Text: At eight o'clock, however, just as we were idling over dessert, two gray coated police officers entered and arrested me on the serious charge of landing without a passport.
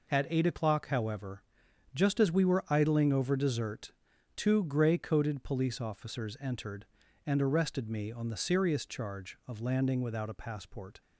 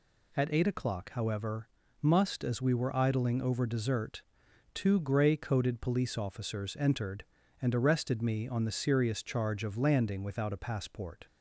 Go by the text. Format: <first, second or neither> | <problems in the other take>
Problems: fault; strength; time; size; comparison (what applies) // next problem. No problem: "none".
first | says "must" for "just"; at 2.0 s